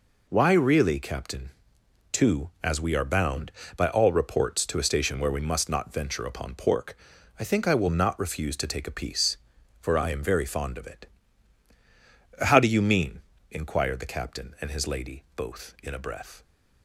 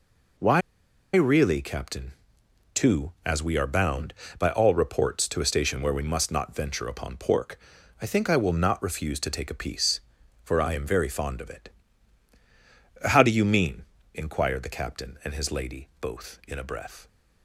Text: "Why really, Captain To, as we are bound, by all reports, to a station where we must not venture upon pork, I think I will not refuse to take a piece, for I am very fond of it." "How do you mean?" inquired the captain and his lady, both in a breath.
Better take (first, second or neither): first